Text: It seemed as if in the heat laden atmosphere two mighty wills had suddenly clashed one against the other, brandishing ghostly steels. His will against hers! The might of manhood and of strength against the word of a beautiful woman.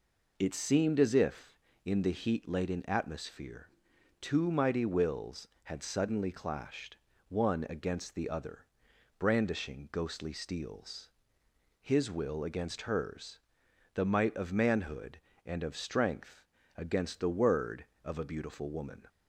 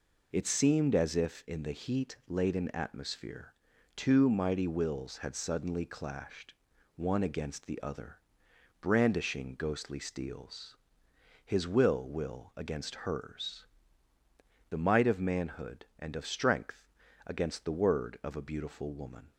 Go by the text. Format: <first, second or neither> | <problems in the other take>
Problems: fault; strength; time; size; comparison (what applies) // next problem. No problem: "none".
first | pauses between "atmosphere" and "two"; at 3.5 s; 0.44 s long; noticeable in the first // pauses between "clashed" and "one"; at 6.5 s; 0.42 s long; slight in the first // says "will" twice; at 12.0 s // pauses between "strength" and "against"; at 16.8 s; 0.38 s long; slight in the first